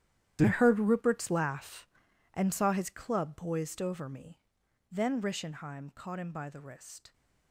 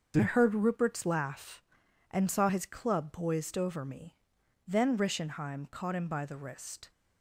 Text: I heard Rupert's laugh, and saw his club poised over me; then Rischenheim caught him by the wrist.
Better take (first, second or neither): second